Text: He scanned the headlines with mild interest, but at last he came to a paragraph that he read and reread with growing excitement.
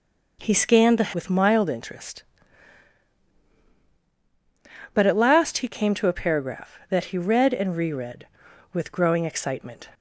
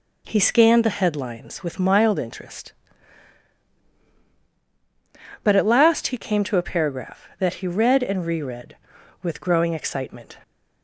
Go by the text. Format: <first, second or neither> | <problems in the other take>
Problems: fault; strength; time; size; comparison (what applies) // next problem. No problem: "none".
second | skips "headlines"; at 1.1 s